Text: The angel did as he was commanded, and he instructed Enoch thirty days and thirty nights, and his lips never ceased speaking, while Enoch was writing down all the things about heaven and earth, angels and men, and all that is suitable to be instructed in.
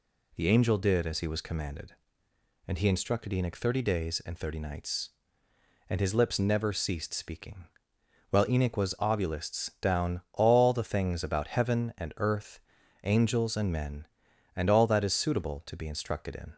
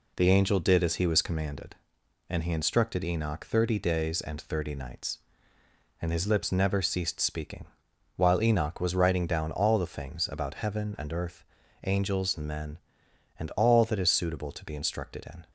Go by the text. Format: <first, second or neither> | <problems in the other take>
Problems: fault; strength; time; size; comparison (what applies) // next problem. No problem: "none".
second | says "ovulists" for "writing"; at 8.9 s